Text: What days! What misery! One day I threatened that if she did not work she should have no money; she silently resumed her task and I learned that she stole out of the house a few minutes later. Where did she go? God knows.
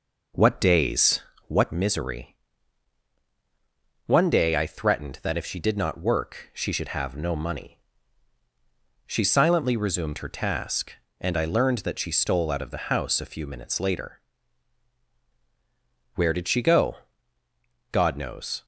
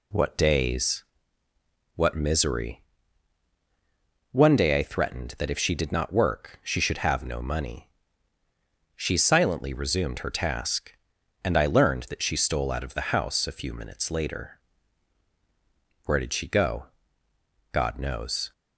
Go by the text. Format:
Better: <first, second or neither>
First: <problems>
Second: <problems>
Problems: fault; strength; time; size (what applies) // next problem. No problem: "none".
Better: second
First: starts louder than the rest; noticeable; until 1.8 s; 5.5 dB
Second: none